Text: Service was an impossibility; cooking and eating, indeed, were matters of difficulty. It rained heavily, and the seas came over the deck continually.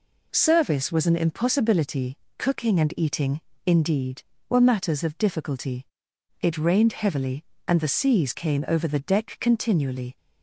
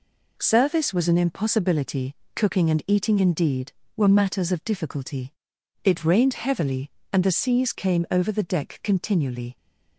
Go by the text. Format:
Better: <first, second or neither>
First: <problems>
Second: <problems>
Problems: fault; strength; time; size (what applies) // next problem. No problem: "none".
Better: neither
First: none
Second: none